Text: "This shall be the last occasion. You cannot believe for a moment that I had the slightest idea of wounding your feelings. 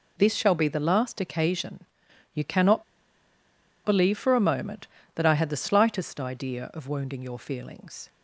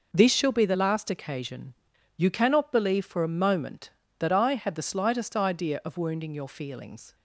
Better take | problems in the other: second | pauses between "cannot" and "believe"; at 2.8 s; 1.0 s long

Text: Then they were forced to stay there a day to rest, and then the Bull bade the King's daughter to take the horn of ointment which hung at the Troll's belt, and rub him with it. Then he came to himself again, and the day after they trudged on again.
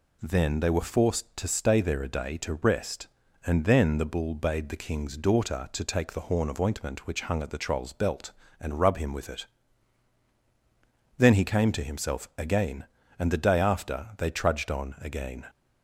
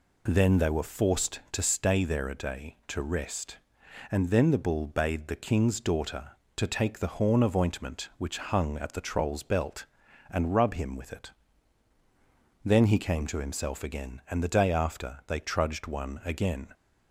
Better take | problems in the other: first | says "one" for "on"; at 15.8 s

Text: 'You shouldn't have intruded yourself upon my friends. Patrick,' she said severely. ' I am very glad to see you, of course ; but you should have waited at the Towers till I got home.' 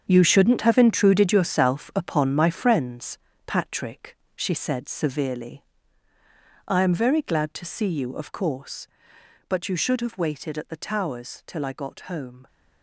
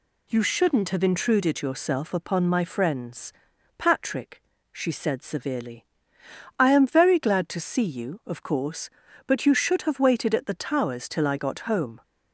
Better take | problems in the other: second | gets quieter; strong; throughout; 11.5 dB

